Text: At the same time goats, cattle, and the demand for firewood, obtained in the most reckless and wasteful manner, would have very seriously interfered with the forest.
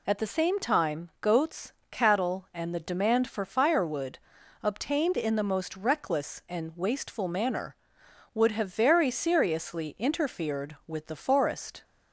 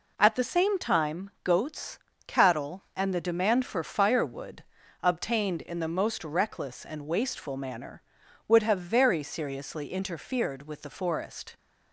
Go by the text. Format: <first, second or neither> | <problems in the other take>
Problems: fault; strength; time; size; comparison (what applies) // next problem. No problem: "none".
neither | none